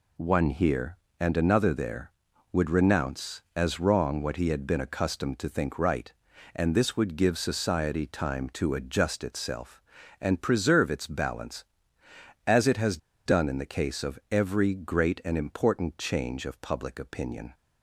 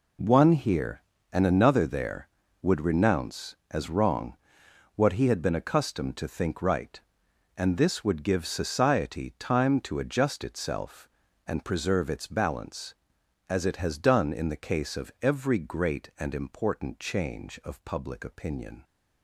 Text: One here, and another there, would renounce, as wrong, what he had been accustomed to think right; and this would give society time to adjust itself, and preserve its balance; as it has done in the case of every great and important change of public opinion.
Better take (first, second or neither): second